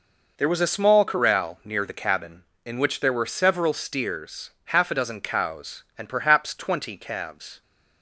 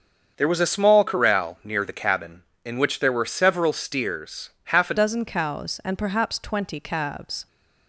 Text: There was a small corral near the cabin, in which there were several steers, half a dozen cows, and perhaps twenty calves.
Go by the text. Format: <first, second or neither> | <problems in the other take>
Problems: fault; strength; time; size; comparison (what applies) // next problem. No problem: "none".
first | starts louder than the rest; until 1.3 s; 7 dB // changes voice at "dozen"; from 4.9 s on; 2.5 s long